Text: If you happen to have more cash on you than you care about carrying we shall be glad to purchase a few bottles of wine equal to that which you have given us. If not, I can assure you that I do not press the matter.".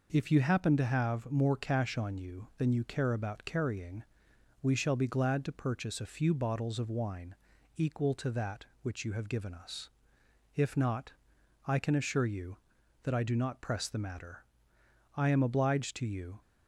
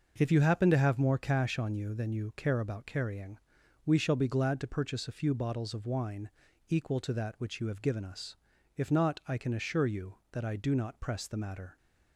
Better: second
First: pauses between "carrying" and "we"; noticeable; at 4.0 s; 0.58 s long // pauses between "wine" and "equal"; at 7.3 s; 0.44 s long // goes on to say "I am obliged to you"; noticeable; from 15.1 s on; 1.2 s long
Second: pauses between "carrying" and "we"; noticeable; at 3.3 s; 0.48 s long // pauses between "wine" and "equal"; at 6.3 s; 0.38 s long

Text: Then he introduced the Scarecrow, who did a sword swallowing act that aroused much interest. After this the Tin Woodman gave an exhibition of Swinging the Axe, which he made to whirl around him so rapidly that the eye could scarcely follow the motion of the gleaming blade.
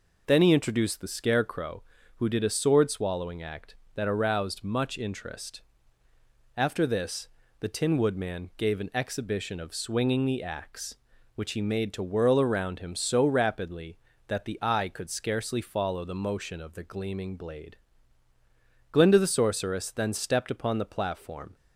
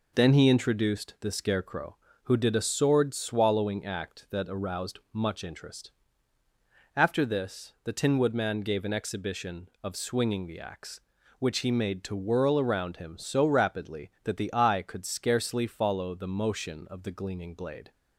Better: second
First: pauses between "this" and "the"; slight; at 7.2 s; 0.32 s long // goes on to say "Glinda the Sorceress then stepped upon the platform"; strong; from 18.9 s on; 2.6 s long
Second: none

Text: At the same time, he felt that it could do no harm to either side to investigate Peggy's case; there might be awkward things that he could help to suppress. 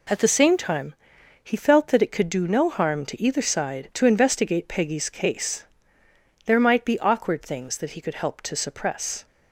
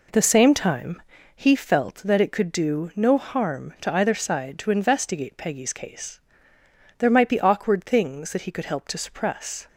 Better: neither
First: none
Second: none

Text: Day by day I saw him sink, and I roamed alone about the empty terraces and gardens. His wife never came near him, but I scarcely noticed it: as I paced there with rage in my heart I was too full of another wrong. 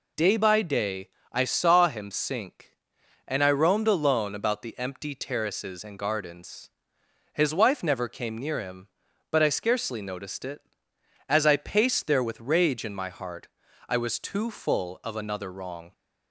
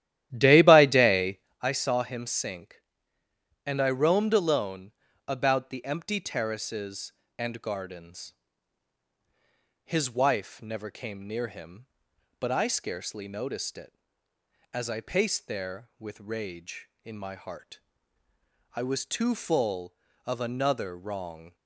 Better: first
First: pauses between "day" and "I"; slight; at 1.0 s; 0.24 s long // pauses between "heart" and "I"; at 13.4 s; 0.42 s long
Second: starts louder than the rest; strong; until 1.7 s; 12.5 dB // pauses between "day" and "I"; slight; at 1.3 s; 0.22 s long // pauses between "alone" and "about"; slight; at 4.9 s; 0.34 s long // pauses between "heart" and "I"; noticeable; at 17.8 s; 0.92 s long

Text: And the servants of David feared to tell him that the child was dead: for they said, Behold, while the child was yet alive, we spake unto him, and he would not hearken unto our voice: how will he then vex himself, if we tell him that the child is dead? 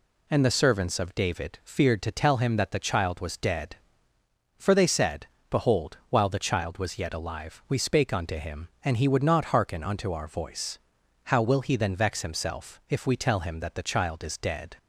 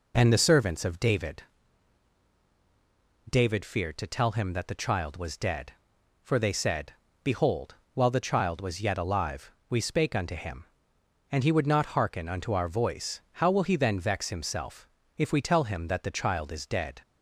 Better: first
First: none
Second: says "David" twice; at 3.2 s

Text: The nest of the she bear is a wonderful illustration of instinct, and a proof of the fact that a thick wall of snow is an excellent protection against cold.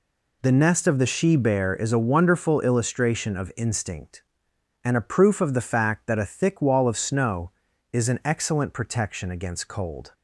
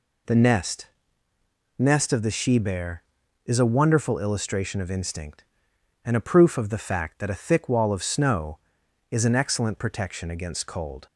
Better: first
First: none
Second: says "nest" twice; at 1.7 s

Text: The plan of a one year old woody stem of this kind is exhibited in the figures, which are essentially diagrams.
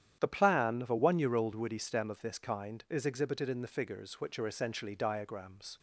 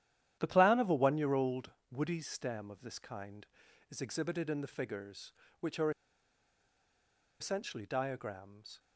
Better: first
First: starts louder than the rest; strong; until 1.2 s; 10 dB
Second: starts louder than the rest; strong; until 1.4 s; 11 dB // pauses between "old" and "woody"; slight; at 1.7 s; 0.18 s long // pauses between "are" and "essentially"; strong; at 5.8 s; 1.5 s long

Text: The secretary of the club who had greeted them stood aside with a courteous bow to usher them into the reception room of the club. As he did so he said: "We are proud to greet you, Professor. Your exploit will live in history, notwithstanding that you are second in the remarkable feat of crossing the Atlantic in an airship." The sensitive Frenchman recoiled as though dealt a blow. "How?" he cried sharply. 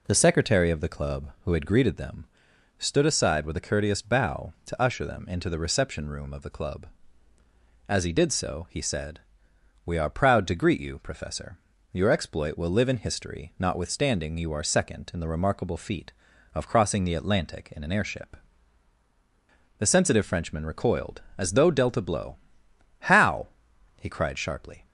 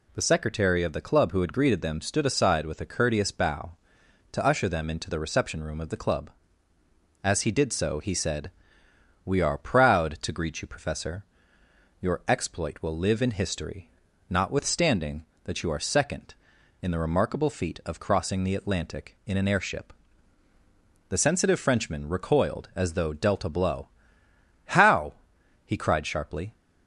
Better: second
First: pauses between "them" and "stood"; noticeable; at 2.2 s; 0.50 s long // skips "that"; at 14.3 s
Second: none

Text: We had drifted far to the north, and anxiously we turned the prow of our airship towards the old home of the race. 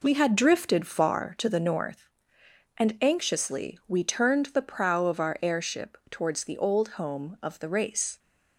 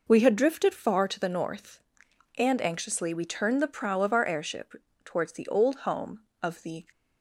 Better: first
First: none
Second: pauses between "airship" and "towards"; slight; at 4.7 s; 0.30 s long // stops before "race"; at 6.9 s

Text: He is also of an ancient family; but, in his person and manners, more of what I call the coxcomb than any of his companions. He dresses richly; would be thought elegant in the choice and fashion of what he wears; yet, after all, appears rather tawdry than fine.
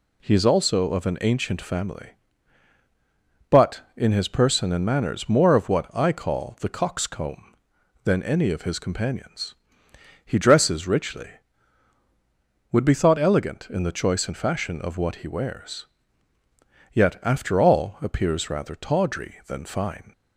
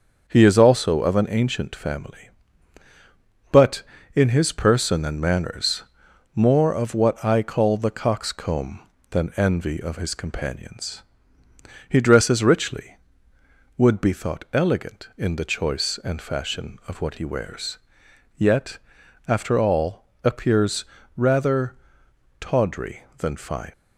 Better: first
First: none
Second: starts louder than the rest; until 1.3 s; 6.5 dB // says "envy" for "any"; at 9.3 s // pauses between "appears" and "rather"; slight; at 20.8 s; 0.32 s long // pauses between "rather" and "tawdry"; noticeable; at 21.7 s; 0.64 s long

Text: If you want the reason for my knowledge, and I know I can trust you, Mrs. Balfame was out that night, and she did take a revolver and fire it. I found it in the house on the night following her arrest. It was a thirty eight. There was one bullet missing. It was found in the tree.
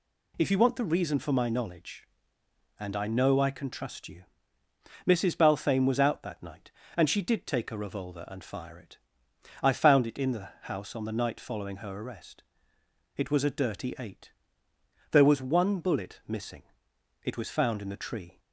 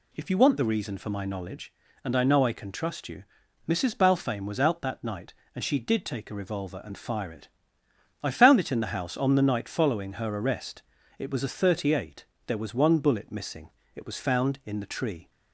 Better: second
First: says "dirty" for "thirty"; at 13.4 s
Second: none

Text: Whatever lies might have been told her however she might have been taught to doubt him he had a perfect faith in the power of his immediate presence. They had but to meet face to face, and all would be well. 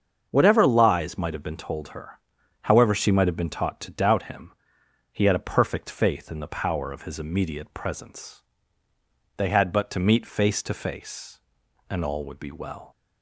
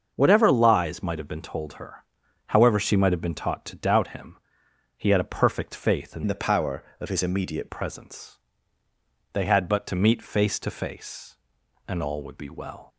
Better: first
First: starts louder than the rest; until 1.3 s; 7 dB // pauses between "her" and "however"; at 2.1 s; 0.44 s long // pauses between "him" and "he"; noticeable; at 4.5 s; 0.62 s long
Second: starts louder than the rest; until 1.1 s; 6.5 dB // pauses between "her" and "however"; at 2.0 s; 0.44 s long // pauses between "him" and "he"; noticeable; at 4.3 s; 0.62 s long // changes voice from "the" to "immediate"; from 6.2 to 7.6 s; 1.4 s long

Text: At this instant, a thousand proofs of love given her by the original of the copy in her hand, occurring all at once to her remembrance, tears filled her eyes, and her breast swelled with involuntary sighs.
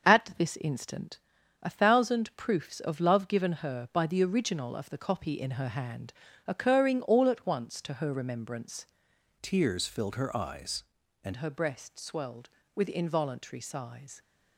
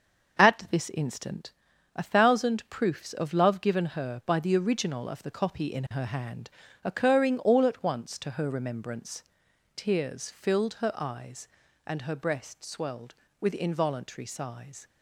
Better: second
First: starts louder than the rest; until 1.1 s; 6.5 dB // changes voice from "tears" to "and"; from 9.4 to 11.3 s; 1.9 s long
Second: starts louder than the rest; until 1.4 s; 6.5 dB

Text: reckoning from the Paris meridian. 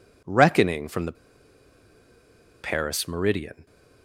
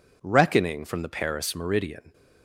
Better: second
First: pauses between "the" and "Paris"; strong; at 1.1 s; 1.4 s long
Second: none

